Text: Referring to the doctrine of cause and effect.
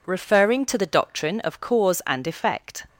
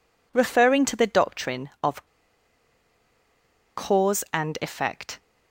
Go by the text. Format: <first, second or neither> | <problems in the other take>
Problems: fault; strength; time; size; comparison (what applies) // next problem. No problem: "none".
first | pauses between "of" and "cause"; strong; at 2.0 s; 1.7 s long